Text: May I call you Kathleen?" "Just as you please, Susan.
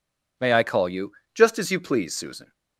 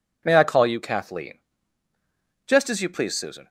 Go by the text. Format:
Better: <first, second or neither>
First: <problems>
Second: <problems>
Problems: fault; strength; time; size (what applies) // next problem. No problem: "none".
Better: second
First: skips "Kathleen"; at 1.2 s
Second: none